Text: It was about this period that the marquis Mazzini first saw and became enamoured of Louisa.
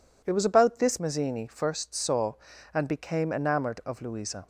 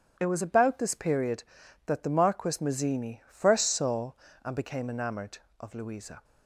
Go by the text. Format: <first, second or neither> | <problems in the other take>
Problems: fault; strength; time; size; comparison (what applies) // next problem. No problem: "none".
second | skips "period that the marquis"; at 0.9 s